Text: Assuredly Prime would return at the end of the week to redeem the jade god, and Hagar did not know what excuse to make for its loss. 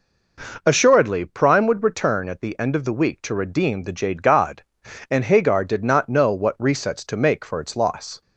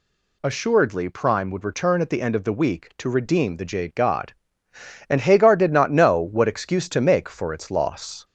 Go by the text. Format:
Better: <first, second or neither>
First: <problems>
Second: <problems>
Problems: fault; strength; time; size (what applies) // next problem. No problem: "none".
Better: second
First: says "resets" for "excuse"; at 6.5 s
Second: none